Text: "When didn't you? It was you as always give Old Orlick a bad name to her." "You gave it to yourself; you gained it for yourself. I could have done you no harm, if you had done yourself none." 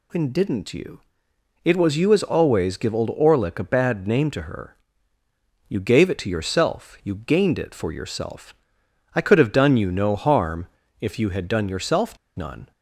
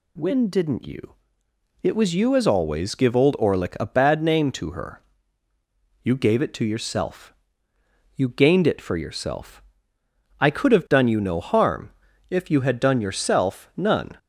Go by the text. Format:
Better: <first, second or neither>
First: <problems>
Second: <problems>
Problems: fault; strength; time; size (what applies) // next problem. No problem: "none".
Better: second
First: pauses between "yourself" and "none"; slight; at 12.1 s; 0.20 s long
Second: none